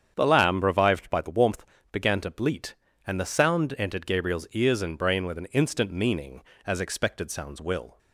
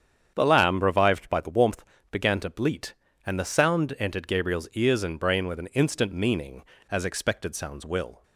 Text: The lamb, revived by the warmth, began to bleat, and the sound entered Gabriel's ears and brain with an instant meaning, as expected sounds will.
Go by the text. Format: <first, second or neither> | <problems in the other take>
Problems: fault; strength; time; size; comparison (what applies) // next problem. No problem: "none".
neither | starts louder than the rest; strong; the same in both